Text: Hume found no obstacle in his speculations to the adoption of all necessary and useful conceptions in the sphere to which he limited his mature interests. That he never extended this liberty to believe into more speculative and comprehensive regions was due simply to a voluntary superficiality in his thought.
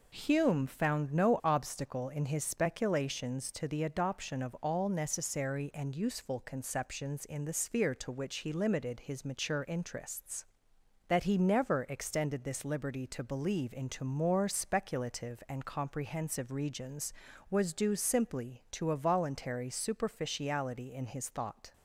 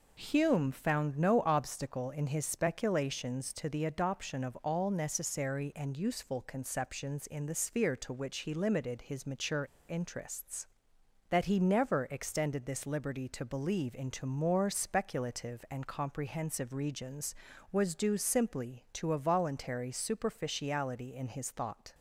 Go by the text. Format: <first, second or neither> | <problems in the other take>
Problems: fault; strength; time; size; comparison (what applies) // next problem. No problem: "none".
first | pauses between "mature" and "interests"; slight; at 9.6 s; 0.26 s long